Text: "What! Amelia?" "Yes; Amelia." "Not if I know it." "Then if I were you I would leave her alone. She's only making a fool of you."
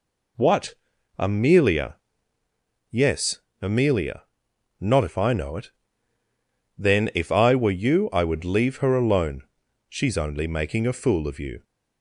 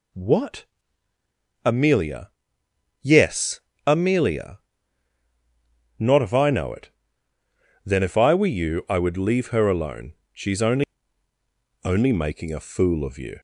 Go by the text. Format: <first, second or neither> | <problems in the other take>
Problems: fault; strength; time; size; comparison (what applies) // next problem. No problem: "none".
first | says "only" twice; at 11.8 s